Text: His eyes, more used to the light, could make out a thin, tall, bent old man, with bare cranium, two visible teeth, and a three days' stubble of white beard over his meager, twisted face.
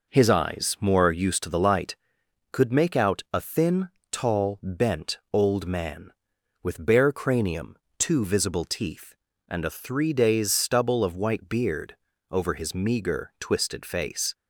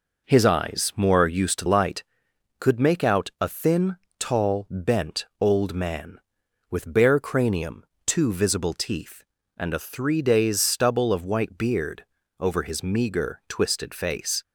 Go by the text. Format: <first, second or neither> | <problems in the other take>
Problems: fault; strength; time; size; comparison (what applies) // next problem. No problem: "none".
first | skips "the"; at 1.6 s // pauses between "beard" and "over"; slight; at 12.0 s; 0.34 s long; slight in the first